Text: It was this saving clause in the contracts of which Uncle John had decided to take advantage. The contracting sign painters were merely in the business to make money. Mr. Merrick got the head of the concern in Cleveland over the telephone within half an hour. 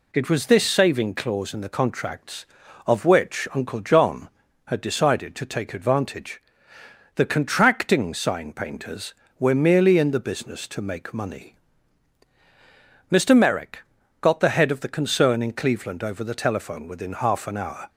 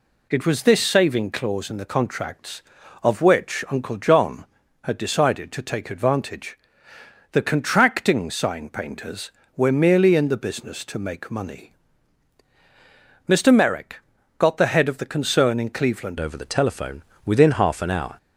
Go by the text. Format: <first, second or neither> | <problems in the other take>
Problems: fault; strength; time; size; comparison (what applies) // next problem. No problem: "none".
first | pauses between "Merrick" and "got"; at 14.0 s; 0.38 s long; also in the first // changes voice at "over"; from 16.1 s on; 2.0 s long // pauses between "telephone" and "within"; slight; at 17.0 s; 0.24 s long